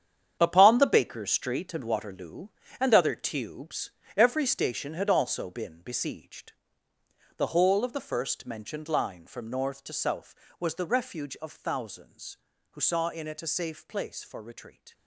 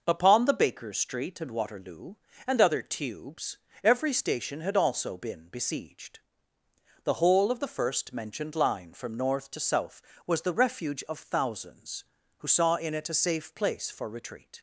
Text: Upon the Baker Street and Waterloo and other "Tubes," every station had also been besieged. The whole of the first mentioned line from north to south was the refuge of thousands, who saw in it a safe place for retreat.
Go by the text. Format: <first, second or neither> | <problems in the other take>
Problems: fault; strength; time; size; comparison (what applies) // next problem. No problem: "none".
second | gets quieter; strong; throughout; 11.5 dB